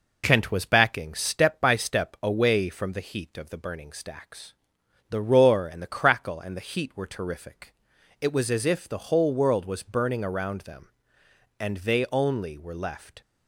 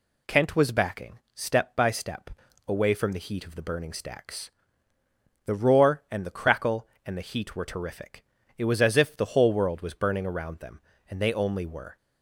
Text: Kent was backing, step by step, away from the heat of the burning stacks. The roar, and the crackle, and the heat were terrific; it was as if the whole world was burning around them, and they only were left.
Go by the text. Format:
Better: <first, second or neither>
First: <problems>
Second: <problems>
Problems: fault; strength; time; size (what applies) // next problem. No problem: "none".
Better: first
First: none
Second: stops before "left"; at 11.9 s